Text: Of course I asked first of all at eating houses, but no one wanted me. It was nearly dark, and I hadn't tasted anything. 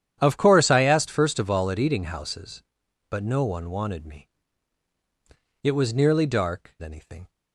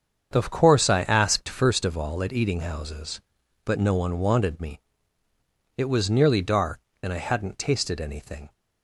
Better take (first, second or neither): second